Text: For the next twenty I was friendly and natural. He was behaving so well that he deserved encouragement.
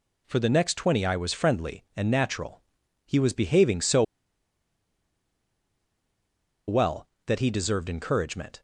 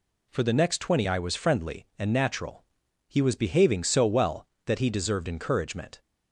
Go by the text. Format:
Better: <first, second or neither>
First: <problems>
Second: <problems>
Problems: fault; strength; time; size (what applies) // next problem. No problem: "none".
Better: second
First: pauses between "so" and "well"; strong; at 4.0 s; 2.6 s long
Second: none